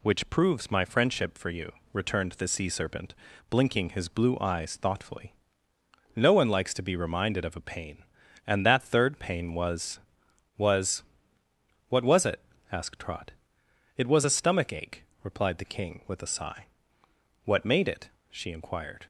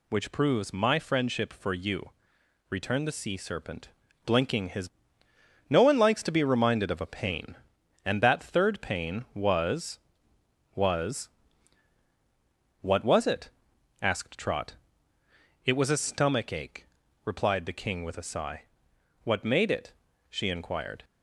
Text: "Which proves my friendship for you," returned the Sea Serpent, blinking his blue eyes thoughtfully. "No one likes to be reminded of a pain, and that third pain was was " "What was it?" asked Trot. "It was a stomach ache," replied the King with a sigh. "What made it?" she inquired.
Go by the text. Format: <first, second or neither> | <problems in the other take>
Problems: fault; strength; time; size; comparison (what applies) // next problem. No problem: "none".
first | skips "blue eyes thoughtfully"; at 5.2 s